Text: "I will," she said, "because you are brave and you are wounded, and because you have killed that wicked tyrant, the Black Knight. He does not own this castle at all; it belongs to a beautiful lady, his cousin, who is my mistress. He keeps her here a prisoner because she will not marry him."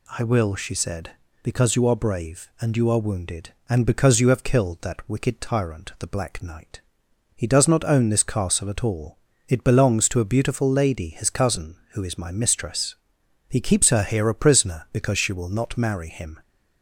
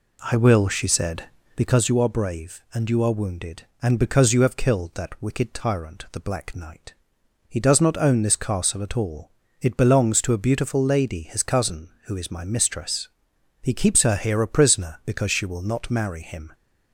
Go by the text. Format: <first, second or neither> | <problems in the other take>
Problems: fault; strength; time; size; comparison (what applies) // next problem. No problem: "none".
first | starts louder than the rest; slight; until 1.9 s; 3 dB